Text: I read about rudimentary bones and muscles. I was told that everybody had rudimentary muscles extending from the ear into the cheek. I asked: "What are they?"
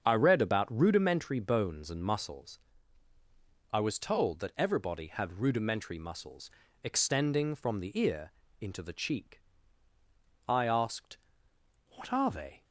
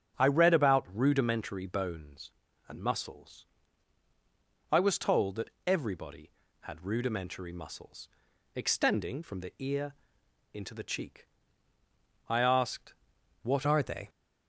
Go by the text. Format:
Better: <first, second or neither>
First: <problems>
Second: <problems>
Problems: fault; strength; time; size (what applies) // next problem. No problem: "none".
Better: first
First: starts louder than the rest; strong; until 1.0 s; 7 dB // pauses between "muscles" and "extending"; slight; at 6.5 s; 0.32 s long // pauses between "ear" and "into"; slight; at 8.3 s; 0.28 s long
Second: starts louder than the rest; strong; until 1.2 s; 8.5 dB // pauses between "that" and "everybody"; slight; at 5.4 s; 0.16 s long // pauses between "muscles" and "extending"; noticeable; at 8.0 s; 0.46 s long // pauses between "ear" and "into"; noticeable; at 9.9 s; 0.58 s long // changes voice at "are"; from 13.6 s on; 0.4 s long